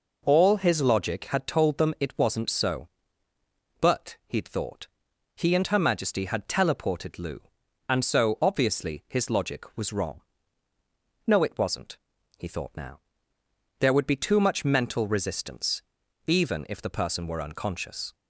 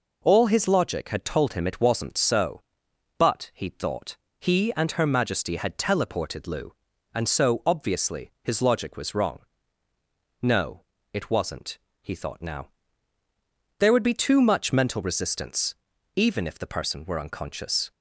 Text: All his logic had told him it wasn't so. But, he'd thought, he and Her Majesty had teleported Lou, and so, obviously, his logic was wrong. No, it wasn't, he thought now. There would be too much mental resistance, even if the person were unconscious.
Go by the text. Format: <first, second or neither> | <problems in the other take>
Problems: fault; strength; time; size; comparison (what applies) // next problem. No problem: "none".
second | says "them" for "him"; at 1.7 s